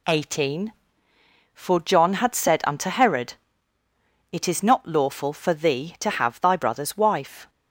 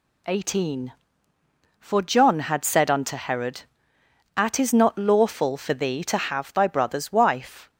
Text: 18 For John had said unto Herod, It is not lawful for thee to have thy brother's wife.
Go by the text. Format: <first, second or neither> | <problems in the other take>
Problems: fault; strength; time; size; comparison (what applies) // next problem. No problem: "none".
first | says "At" for "It"; at 4.3 s